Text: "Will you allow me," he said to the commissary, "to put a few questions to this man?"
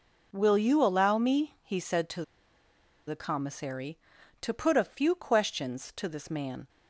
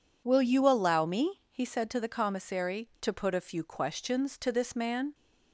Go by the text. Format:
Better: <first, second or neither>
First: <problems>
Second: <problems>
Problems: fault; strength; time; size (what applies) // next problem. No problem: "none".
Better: second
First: pauses between "to" and "the"; noticeable; at 2.2 s; 0.85 s long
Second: none